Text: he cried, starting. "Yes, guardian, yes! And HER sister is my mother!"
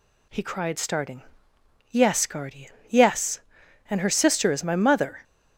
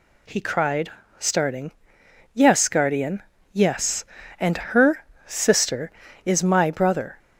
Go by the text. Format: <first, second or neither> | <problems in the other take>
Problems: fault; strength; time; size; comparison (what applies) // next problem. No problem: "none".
first | pauses between "HER" and "sister"; slight; at 5.0 s; 0.20 s long // says "brother" for "mother"; at 6.6 s